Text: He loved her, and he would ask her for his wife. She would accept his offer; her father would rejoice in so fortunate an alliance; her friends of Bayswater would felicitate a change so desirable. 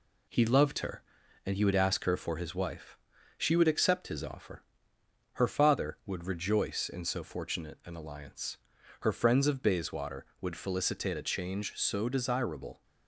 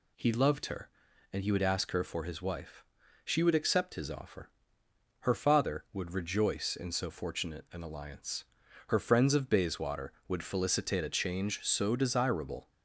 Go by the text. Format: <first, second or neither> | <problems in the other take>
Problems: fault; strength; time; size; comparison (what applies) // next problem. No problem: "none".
second | gets quieter; slight; throughout; 2.5 dB